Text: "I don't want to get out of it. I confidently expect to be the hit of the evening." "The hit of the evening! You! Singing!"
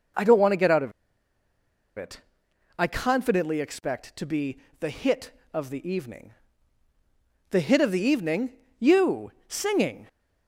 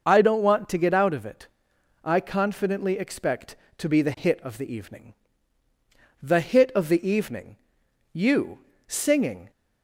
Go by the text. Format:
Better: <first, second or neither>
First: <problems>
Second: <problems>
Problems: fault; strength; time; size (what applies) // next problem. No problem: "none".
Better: second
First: pauses between "of" and "it"; at 0.9 s; 1.0 s long // pauses between "be" and "the"; slight; at 4.5 s; 0.22 s long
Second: none